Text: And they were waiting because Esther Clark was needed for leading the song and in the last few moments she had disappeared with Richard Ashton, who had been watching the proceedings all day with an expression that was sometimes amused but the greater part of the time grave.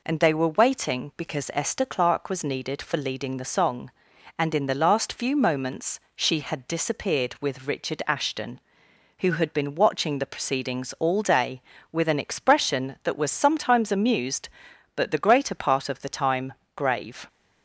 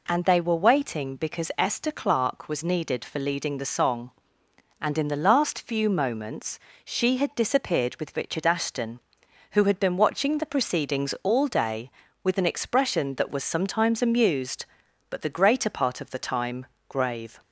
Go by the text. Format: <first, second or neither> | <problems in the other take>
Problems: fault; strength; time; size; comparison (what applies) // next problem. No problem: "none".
neither | pauses between "moments" and "she"; slight; the same in both // pauses between "time" and "grave"; slight; the same in both